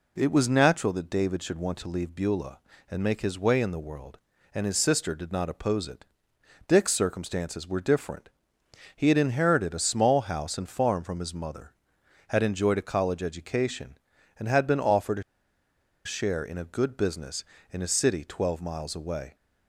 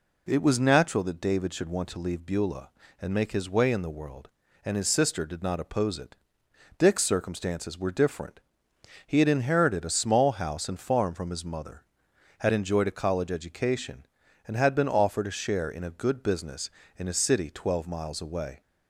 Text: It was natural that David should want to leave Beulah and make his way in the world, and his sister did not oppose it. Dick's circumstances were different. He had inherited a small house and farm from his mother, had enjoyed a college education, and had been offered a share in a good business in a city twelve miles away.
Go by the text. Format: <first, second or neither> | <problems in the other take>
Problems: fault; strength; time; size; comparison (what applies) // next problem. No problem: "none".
second | pauses between "a" and "share"; noticeable; at 15.2 s; 0.82 s long